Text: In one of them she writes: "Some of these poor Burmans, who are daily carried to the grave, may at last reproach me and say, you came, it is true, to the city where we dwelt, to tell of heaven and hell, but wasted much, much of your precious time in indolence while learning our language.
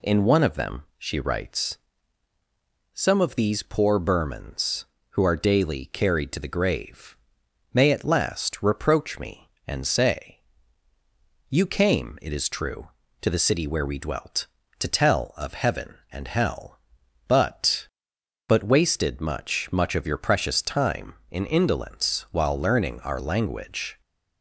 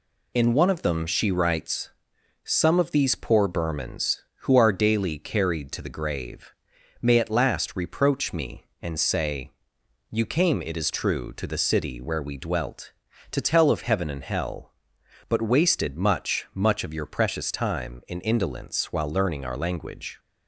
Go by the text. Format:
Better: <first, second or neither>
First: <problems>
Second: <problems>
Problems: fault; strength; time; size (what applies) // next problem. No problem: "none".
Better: second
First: says "but" twice; at 18.4 s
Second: none